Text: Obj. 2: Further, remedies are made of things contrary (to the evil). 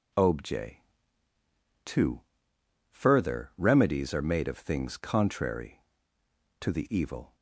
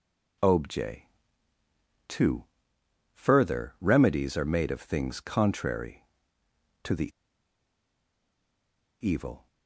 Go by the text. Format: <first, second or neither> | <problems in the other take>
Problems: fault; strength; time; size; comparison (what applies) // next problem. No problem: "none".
first | pauses between "the" and "evil"; strong; at 7.0 s; 1.9 s long